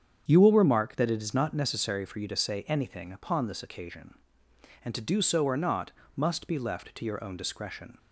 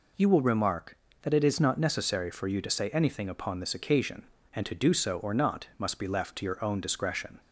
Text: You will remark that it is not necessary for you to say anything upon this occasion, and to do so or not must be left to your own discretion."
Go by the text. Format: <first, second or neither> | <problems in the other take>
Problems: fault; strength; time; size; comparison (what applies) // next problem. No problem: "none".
second | starts louder than the rest; strong; until 1.7 s; 8 dB // pauses between "not" and "must"; slight; at 5.9 s; 0.24 s long